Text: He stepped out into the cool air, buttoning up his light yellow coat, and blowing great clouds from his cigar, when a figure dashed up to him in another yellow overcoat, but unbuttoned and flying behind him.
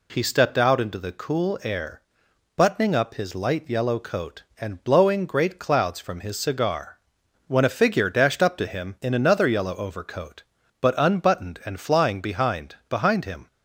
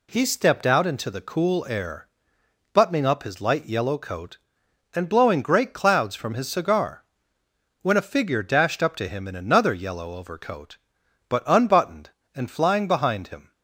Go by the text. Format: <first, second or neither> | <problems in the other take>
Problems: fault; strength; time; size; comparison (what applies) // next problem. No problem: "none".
second | says "behind" twice; at 12.8 s